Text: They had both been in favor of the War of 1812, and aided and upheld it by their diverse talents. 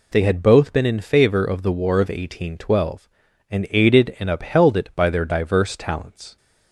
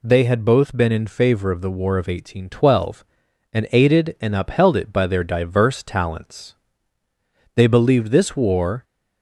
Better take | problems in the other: first | goes on to say "They believed this war"; noticeable; from 7.5 s on; 1.2 s long

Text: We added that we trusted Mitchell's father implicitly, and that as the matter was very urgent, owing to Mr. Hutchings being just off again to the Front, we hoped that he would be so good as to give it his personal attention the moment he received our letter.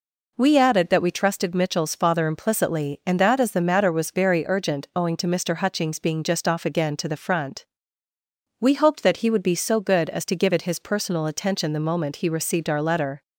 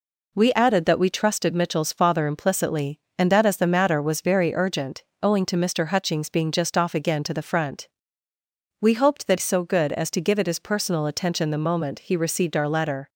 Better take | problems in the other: first | skips "he would be"; at 9.3 s

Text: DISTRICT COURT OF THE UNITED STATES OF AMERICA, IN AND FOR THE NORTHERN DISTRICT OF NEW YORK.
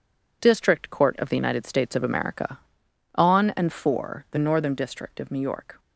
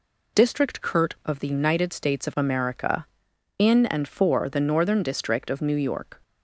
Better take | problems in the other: second | says "On" for "IN"; at 3.1 s

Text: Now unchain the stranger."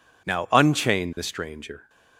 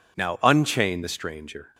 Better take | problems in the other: neither | none

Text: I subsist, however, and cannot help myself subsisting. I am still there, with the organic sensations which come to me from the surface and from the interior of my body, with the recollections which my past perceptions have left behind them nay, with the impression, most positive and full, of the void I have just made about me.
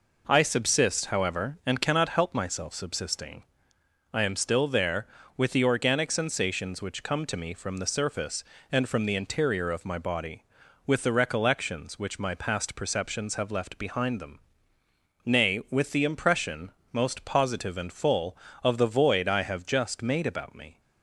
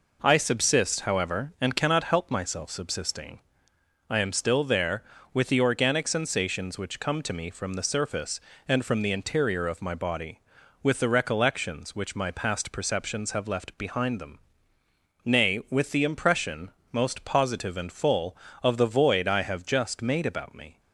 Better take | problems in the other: neither | pauses between "them" and "nay"; noticeable; the same in both

